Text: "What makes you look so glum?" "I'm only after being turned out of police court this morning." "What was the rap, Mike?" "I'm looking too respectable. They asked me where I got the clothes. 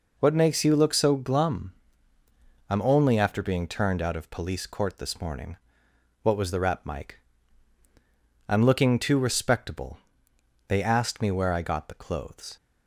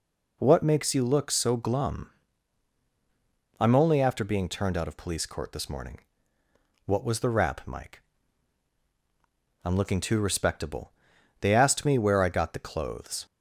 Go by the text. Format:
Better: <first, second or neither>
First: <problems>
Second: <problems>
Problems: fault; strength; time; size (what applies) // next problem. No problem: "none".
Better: neither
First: none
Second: none